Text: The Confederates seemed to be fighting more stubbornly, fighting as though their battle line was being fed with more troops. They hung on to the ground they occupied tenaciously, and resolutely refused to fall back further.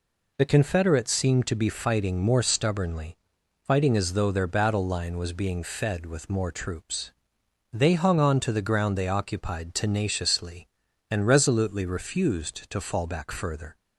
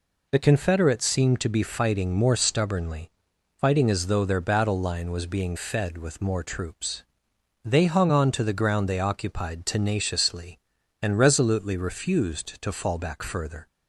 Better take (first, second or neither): neither